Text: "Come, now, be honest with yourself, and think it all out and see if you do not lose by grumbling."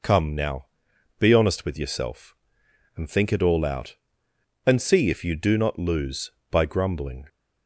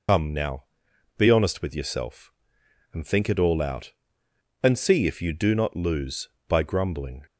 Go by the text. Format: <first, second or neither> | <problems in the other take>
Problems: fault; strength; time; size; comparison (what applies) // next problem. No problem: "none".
first | loses the start of "Come"; at 0.0 s; 80 ms